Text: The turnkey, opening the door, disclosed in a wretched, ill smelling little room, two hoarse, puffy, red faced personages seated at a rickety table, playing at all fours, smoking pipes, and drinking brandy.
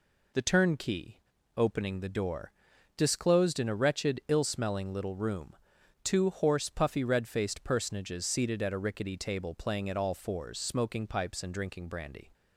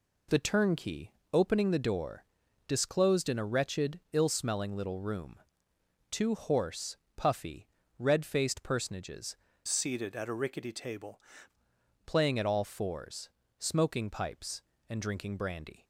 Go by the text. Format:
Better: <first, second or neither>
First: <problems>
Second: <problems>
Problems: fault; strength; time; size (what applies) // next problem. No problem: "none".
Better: first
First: none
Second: changes voice from "seated" to "table"; from 9.6 to 11.2 s; 1.6 s long